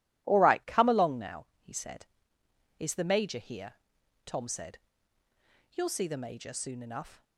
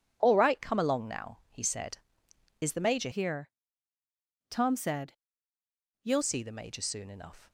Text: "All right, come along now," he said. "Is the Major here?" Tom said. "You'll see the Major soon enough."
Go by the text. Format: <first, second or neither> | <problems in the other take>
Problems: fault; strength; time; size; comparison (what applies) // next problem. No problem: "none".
first | changes voice from "here" to "You'll"; from 3.1 to 6.2 s; 3.1 s long